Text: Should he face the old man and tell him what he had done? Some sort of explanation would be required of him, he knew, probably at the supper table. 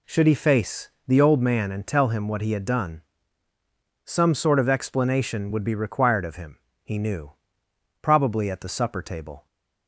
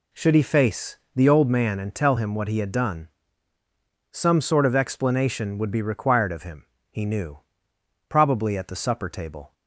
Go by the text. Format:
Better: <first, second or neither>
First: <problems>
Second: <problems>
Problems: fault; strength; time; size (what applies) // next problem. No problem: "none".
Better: neither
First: pauses between "face" and "the"; slight; at 0.9 s; 0.16 s long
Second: pauses between "face" and "the"; slight; at 0.9 s; 0.16 s long